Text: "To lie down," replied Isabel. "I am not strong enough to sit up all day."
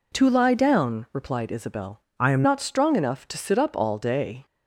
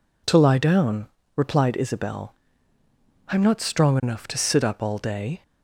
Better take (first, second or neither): second